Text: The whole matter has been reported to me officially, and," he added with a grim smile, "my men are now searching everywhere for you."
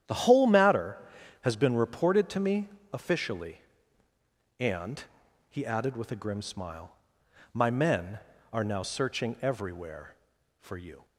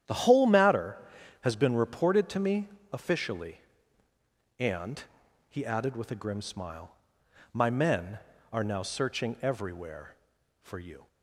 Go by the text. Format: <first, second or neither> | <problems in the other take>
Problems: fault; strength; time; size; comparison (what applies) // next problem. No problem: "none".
neither | starts louder than the rest; strong; the same in both // pauses between "me" and "officially"; slight; the same in both